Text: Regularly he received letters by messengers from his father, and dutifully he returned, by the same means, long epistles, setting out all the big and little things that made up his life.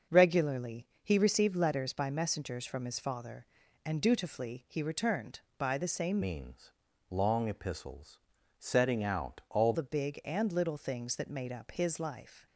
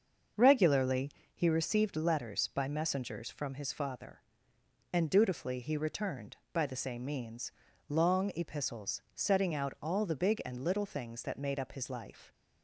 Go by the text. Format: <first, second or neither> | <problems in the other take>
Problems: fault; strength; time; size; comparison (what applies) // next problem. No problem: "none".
second | starts louder than the rest; until 1.2 s; 6 dB; also in the second // pauses between "Regularly" and "he"; slight; at 0.8 s; 0.18 s long; slight in the second // changes voice from "means" to "all"; from 6.2 to 9.7 s; 3.5 s long